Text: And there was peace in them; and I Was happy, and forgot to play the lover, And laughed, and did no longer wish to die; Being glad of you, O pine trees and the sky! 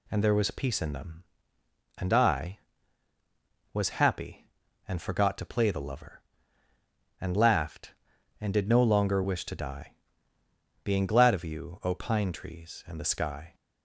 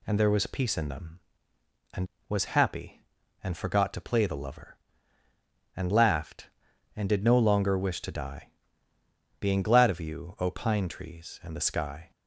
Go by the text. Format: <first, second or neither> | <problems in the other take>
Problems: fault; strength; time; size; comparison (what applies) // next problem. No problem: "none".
first | skips "I"; at 2.1 s